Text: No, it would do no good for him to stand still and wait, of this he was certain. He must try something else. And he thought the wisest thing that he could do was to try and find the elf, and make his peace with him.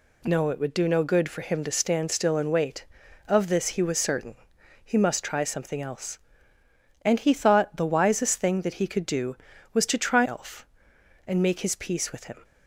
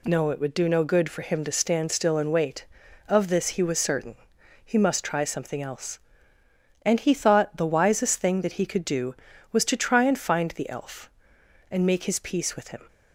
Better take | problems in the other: second | skips "and find the"; at 10.2 s

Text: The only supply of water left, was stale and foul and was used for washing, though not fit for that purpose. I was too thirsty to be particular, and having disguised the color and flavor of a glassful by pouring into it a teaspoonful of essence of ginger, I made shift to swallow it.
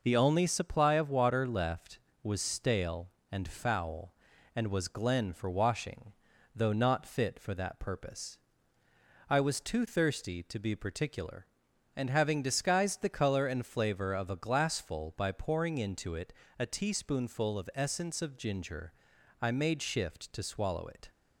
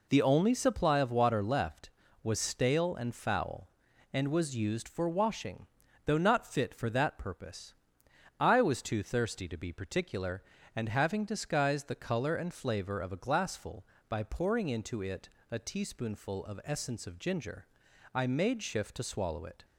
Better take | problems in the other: second | says "glen" for "used"; at 4.8 s // pauses between "it" and "a"; slight; at 16.3 s; 0.26 s long; slight in the second

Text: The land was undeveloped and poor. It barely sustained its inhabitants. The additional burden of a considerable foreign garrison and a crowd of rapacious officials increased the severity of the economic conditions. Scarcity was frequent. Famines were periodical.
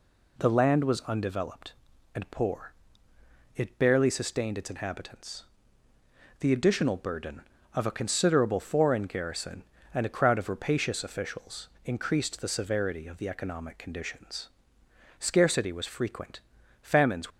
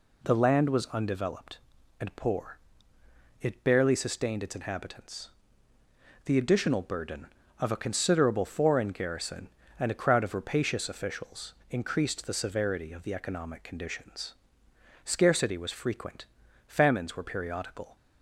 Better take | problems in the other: second | pauses between "officials" and "increased"; slight; at 11.6 s; 0.18 s long; slight in the second // stops before "were periodical"; at 17.2 s

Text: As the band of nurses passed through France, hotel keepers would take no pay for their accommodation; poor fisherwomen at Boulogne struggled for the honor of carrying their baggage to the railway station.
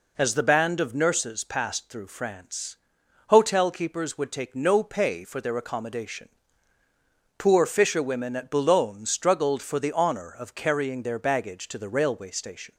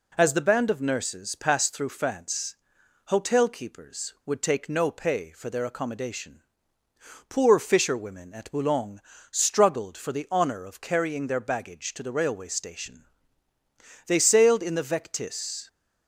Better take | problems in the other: first | pauses between "Boulogne" and "struggled"; slight; at 9.0 s; 0.28 s long // goes on to say "They sailed in the Vectis"; from 14.0 s on; 1.6 s long

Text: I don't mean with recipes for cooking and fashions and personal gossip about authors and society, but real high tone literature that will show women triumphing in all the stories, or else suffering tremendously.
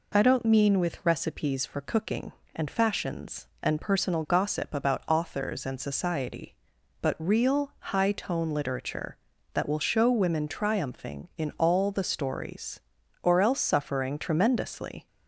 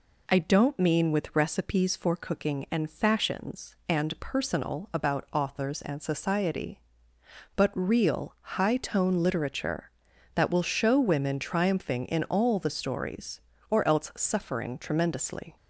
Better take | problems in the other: first | skips "gossip"; at 4.9 s

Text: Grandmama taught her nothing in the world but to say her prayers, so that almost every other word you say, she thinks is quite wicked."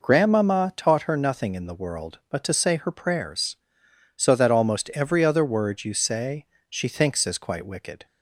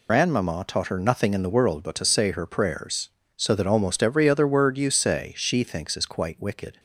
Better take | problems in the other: first | loses the start of "Grandmama"; at 0.0 s; 85 ms

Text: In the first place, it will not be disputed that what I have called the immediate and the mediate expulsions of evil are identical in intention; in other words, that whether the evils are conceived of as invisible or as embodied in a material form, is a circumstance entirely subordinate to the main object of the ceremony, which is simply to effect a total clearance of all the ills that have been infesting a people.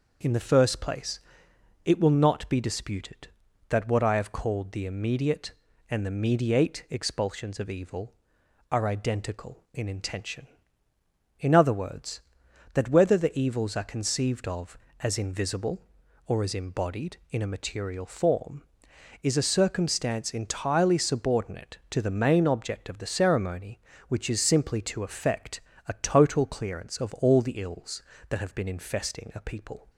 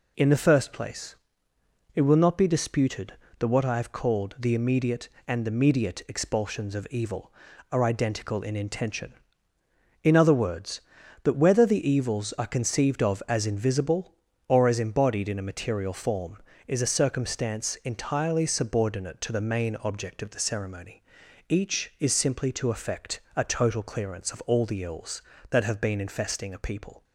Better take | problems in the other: first | says "each" for "which"; at 21.4 s // pauses between "effect" and "a"; slight; at 23.1 s; 0.16 s long; slight in the first

